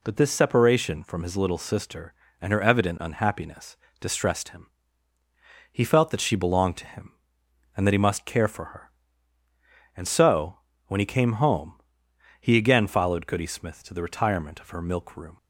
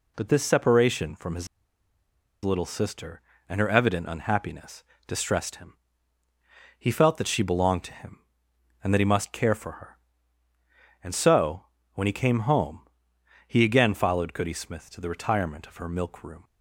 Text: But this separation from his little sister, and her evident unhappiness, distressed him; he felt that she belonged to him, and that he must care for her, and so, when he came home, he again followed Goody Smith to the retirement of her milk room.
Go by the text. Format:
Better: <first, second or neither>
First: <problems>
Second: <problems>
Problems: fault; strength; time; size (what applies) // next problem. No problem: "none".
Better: first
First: none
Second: pauses between "his" and "little"; noticeable; at 1.4 s; 0.96 s long